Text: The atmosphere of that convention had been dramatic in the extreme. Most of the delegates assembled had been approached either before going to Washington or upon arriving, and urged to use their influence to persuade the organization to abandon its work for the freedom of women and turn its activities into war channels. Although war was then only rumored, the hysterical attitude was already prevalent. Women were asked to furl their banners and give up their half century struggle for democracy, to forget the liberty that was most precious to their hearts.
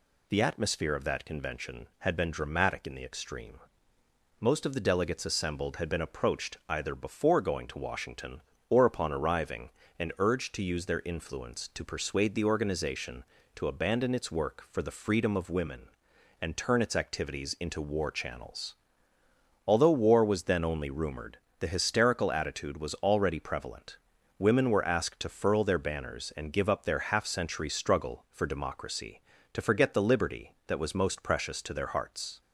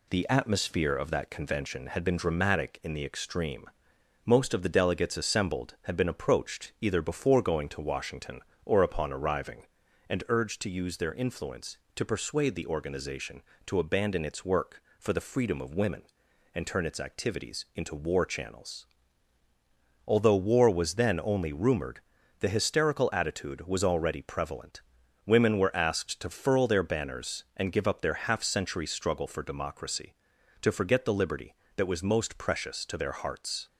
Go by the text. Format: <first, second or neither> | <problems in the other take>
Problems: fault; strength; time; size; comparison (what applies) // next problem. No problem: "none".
neither | none